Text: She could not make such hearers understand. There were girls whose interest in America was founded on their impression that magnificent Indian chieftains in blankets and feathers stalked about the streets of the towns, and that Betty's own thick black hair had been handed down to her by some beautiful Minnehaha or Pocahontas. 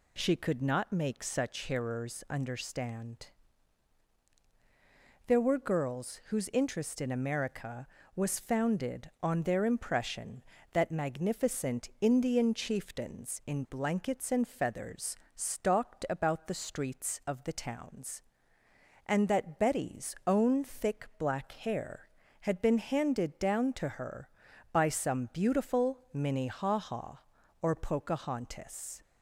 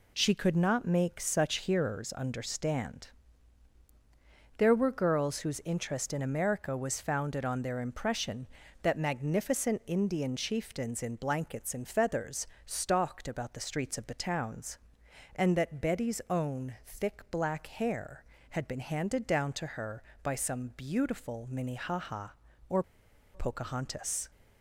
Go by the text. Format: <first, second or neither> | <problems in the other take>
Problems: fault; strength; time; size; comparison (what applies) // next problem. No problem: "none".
first | pauses between "feathers" and "stalked"; slight; at 12.4 s; 0.18 s long; slight in the first // pauses between "or" and "Pocahontas"; noticeable; at 22.8 s; 0.50 s long